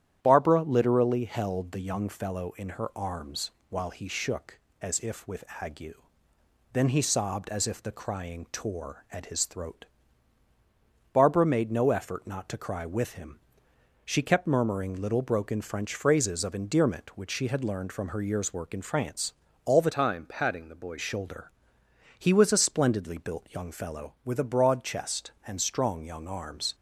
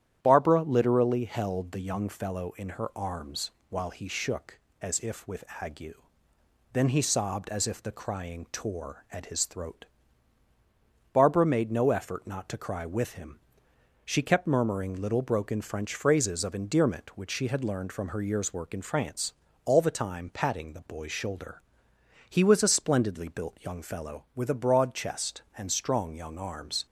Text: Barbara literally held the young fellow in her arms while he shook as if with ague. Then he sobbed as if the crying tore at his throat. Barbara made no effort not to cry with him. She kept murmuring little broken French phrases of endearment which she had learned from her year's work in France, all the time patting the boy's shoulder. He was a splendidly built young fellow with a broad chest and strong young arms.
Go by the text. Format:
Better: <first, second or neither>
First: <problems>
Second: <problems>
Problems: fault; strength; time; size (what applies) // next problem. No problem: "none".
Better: second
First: starts louder than the rest; strong; until 1.2 s; 10.5 dB // pauses between "arms" and "while"; slight; at 3.5 s; 0.20 s long // pauses between "with" and "ague"; slight; at 5.4 s; 0.18 s long // changes voice from "time" to "boy's"; from 19.9 to 20.9 s; 1.0 s long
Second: starts louder than the rest; strong; until 1.2 s; 10.5 dB // pauses between "arms" and "while"; slight; at 3.5 s; 0.20 s long // pauses between "with" and "ague"; slight; at 5.4 s; 0.18 s long